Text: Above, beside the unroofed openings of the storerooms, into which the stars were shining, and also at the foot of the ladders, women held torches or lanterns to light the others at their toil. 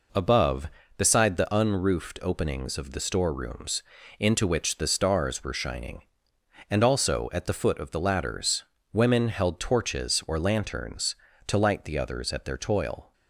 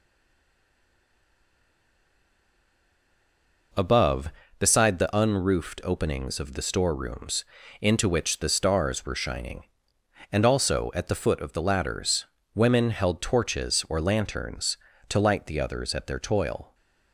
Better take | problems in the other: first | stays silent before the first word; strong; until 3.7 s; 3.7 s long

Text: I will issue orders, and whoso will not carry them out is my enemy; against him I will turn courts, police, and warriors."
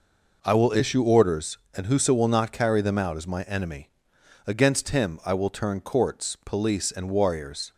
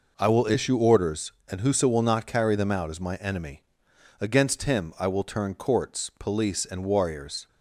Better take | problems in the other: neither | none

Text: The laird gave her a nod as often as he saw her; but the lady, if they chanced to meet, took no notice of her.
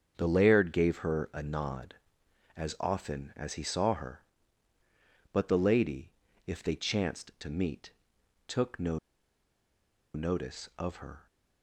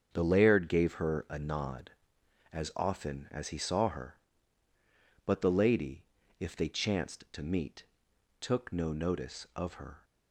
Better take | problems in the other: second | starts louder than the rest; until 1.1 s; 7 dB; also in the second // pauses between "no" and "notice"; at 8.9 s; 1.1 s long

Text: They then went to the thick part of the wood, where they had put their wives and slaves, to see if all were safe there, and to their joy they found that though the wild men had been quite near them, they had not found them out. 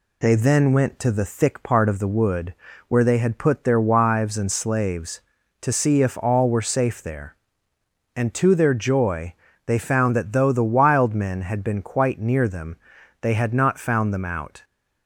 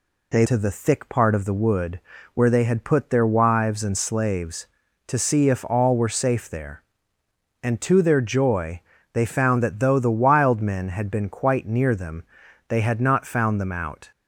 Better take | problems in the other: first | skips "then went"; at 0.4 s // pauses between "joy" and "they"; slight; at 8.8 s; 0.32 s long; slight in the first

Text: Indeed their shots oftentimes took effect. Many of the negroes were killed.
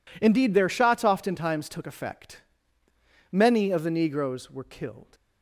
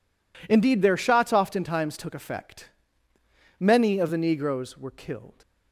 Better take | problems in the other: neither | none

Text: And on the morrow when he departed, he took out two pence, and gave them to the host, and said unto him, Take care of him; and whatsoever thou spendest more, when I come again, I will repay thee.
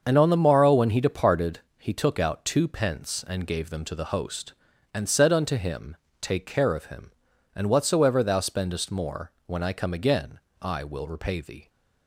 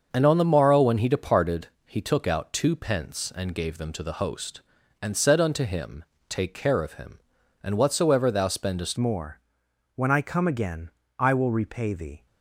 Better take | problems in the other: first | starts louder than the rest; until 1.1 s; 6.5 dB; also in the first // changes voice at "more"; from 8.9 s on; 3.3 s long

